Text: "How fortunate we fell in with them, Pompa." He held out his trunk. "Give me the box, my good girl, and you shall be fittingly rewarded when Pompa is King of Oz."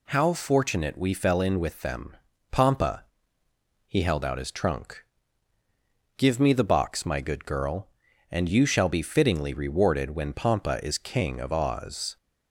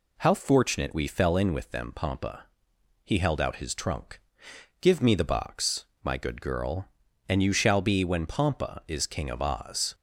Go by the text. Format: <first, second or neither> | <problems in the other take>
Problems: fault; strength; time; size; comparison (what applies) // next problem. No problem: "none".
first | skips "fittingly rewarded"; at 8.0 s